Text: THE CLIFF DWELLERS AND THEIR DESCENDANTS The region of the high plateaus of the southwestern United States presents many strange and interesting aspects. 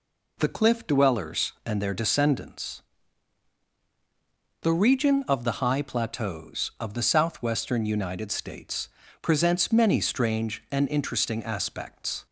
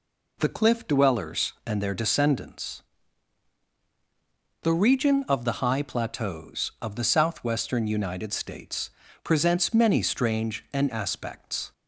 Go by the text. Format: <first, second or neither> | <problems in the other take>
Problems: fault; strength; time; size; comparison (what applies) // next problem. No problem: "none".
first | pauses between "DESCENDANTS" and "The"; strong; at 2.8 s; 1.8 s long; strong in the first // pauses between "States" and "presents"; slight; at 8.8 s; 0.36 s long; slight in the first // skips "interesting"; at 10.8 s